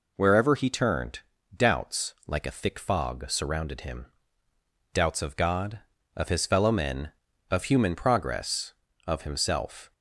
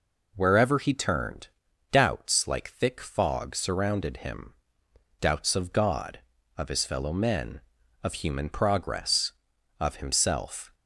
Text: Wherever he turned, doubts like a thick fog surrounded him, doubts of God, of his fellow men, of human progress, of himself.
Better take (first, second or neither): first